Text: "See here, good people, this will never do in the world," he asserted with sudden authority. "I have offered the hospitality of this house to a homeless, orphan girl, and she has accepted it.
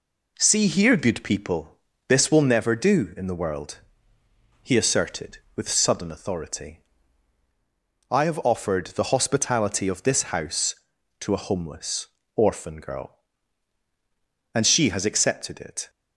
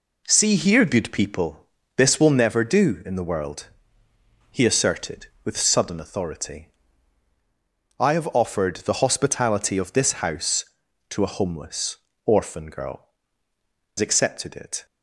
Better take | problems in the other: first | skips "and she has"; at 13.5 s

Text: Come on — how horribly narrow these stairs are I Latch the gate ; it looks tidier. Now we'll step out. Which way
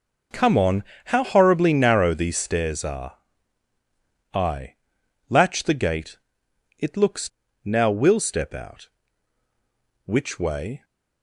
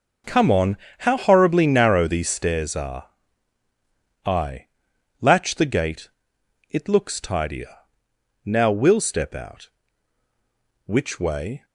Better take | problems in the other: second | pauses between "are" and "I"; at 3.1 s; 1.1 s long; also in the second // pauses between "I" and "Latch"; noticeable; at 4.7 s; 0.54 s long; noticeable in the second // skips "tidier"; at 7.4 s

